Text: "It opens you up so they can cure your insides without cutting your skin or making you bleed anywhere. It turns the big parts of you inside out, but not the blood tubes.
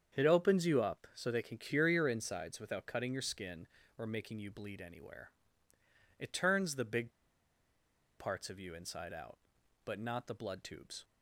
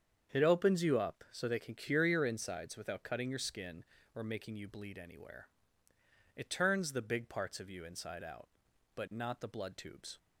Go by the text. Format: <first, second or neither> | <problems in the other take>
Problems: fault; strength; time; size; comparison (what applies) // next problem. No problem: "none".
second | starts louder than the rest; strong; until 1.2 s; 7.5 dB; strong in the second // pauses between "big" and "parts"; at 7.1 s; 1.0 s long